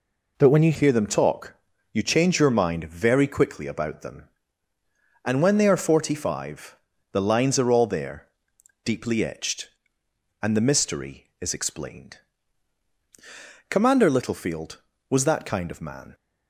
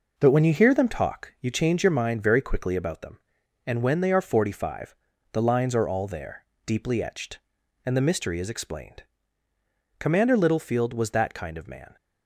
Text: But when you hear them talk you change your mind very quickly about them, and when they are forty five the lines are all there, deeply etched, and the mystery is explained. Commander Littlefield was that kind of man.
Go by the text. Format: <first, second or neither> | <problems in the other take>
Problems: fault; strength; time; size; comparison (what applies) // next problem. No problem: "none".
second | changes voice at "hear"; from 0.7 s on; 15.4 s long // pauses between "talk" and "you"; at 1.5 s; 0.38 s long // pauses between "five" and "the"; slight; at 6.7 s; 0.36 s long; also in the second